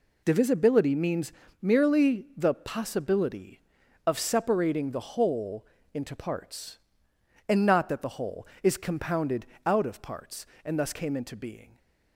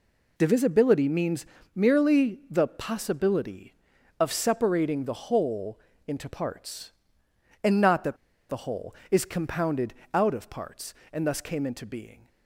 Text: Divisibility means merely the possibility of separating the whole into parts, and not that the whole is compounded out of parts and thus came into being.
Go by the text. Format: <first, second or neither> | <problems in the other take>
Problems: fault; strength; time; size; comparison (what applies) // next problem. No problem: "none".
first | pauses between "means" and "merely"; slight; at 1.4 s; 0.30 s long; slight in the first // pauses between "whole" and "into"; slight; at 5.7 s; 0.28 s long; slight in the first // pauses between "that" and "the"; slight; at 8.1 s; 0.33 s long // pauses between "compounded" and "out"; slight; at 9.9 s; 0.20 s long; slight in the first